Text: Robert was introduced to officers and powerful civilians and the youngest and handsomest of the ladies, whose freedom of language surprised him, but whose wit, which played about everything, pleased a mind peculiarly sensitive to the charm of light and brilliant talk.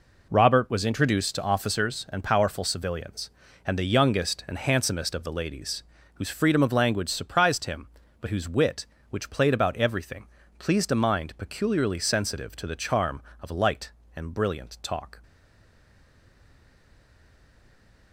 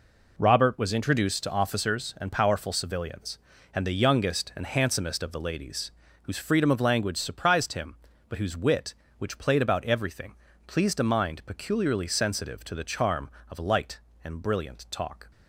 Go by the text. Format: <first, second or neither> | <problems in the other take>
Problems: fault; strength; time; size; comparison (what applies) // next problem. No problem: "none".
second | stays silent after the last word; strong; from 15.2 s on; 2.9 s long